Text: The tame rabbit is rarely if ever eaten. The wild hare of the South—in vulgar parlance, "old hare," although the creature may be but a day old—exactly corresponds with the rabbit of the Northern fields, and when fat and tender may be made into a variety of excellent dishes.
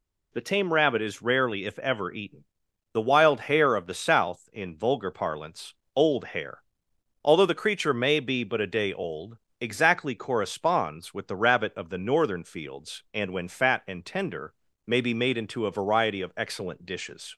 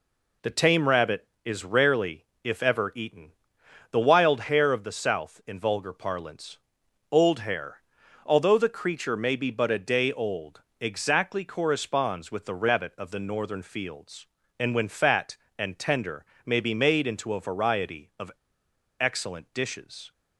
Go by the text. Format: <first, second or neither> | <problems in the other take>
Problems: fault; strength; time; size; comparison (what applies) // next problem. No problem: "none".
first | pauses between "rarely" and "if"; slight; at 2.2 s; 0.22 s long // pauses between "tender" and "may"; slight; at 16.2 s; 0.22 s long; slight in the first // pauses between "of" and "excellent"; noticeable; at 18.3 s; 0.68 s long